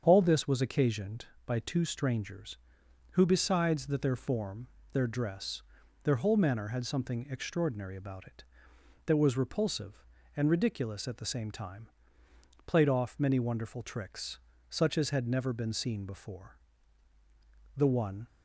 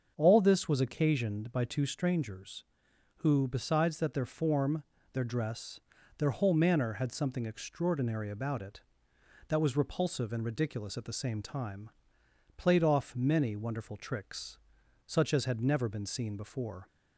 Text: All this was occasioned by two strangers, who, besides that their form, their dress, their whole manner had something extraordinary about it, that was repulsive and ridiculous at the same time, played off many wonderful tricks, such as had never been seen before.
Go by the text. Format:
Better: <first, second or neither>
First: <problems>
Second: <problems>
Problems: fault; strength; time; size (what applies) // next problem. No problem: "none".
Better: second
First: starts louder than the rest; strong; until 1.0 s; 7.5 dB // goes on to say "The one"; from 17.7 s on; 0.50 s long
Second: starts louder than the rest; until 1.1 s; 6.5 dB